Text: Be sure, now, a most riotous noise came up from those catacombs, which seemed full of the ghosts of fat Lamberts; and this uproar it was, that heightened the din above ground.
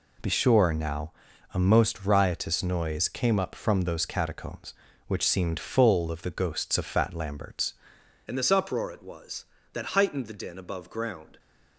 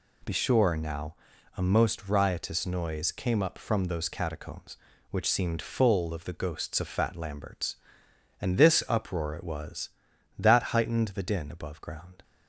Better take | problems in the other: second | changes voice at "and"; from 8.2 s on; 3.1 s long

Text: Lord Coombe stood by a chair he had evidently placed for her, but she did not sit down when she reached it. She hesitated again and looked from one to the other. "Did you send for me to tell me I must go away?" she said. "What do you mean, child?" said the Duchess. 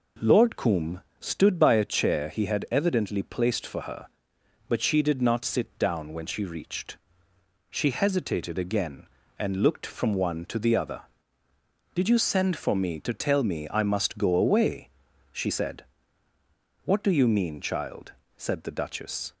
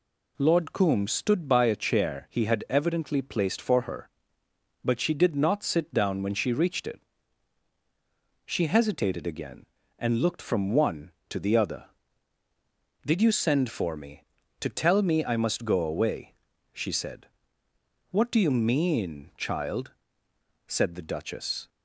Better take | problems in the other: second | pauses between "Coombe" and "stood"; slight; at 1.0 s; 0.18 s long // skips "it"; at 7.3 s

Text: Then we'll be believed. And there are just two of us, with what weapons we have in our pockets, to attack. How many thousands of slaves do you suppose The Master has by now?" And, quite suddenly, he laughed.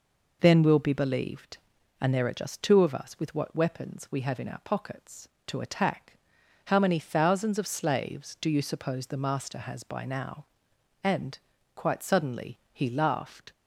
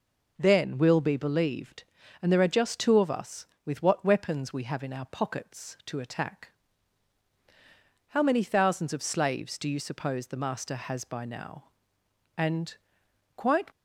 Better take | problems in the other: first | stops before "suddenly he laughed"; at 13.7 s

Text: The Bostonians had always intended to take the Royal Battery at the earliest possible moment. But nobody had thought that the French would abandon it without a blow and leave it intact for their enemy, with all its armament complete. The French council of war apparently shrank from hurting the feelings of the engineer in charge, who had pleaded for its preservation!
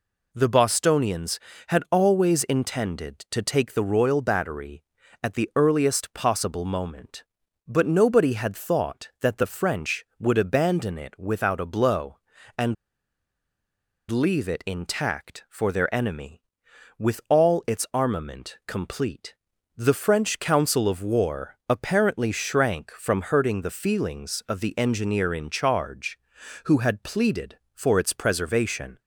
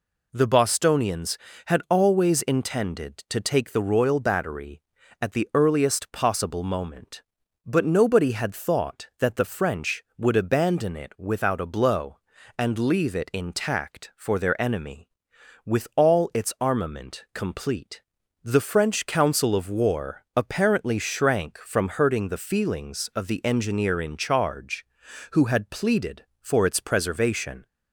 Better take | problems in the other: second | pauses between "and" and "leave"; strong; at 12.7 s; 1.3 s long

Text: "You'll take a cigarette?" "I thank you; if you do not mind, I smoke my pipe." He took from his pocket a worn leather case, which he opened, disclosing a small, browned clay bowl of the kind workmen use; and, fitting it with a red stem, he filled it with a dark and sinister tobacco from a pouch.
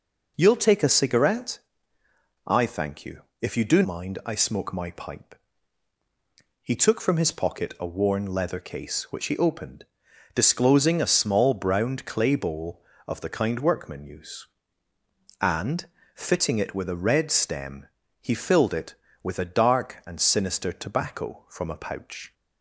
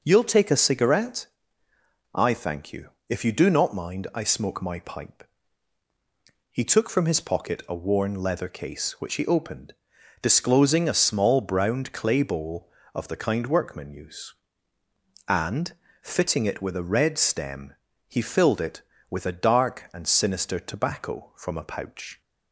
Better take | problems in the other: second | skips "not"; at 3.8 s

